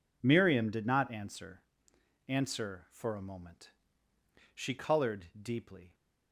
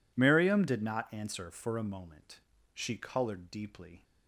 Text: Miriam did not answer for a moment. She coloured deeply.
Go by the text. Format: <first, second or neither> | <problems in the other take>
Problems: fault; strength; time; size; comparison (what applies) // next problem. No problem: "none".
second | says "answer" twice; at 2.2 s // pauses between "coloured" and "deeply"; slight; at 5.2 s; 0.16 s long